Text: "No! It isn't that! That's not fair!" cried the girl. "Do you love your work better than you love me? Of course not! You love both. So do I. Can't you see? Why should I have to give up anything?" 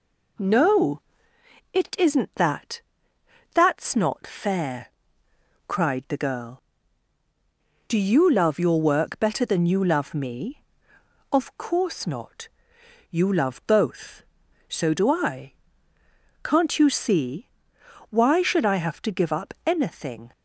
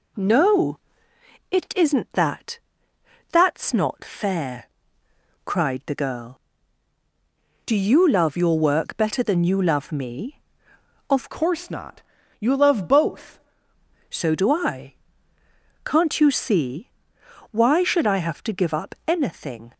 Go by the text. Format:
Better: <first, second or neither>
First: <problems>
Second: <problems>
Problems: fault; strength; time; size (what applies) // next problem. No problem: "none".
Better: first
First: none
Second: changes voice from "course" to "both"; from 11.3 to 13.3 s; 2.0 s long